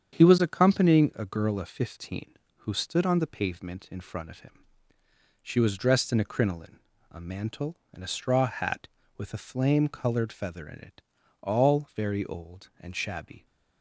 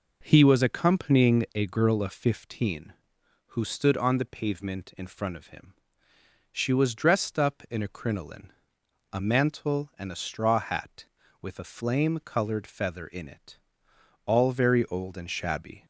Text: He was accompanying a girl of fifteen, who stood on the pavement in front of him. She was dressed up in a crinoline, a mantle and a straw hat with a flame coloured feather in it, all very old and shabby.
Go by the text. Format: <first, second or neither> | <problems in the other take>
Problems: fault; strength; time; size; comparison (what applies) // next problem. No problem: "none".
second | starts louder than the rest; strong; until 1.2 s; 8 dB // skips "up"; at 6.1 s